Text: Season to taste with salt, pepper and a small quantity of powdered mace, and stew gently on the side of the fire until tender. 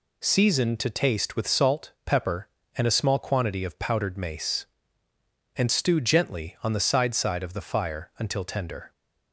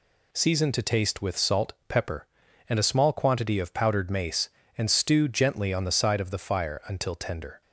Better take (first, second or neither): second